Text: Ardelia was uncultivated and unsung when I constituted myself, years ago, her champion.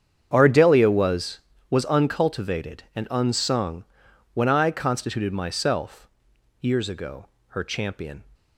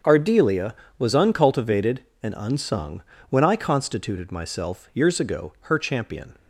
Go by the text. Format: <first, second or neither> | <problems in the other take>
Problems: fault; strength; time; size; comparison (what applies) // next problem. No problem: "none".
second | starts louder than the rest; strong; until 1.3 s; 8 dB; strong in the second // says "was" twice; at 1.6 s // pauses between "unsung" and "when"; noticeable; at 3.8 s; 0.50 s long; slight in the second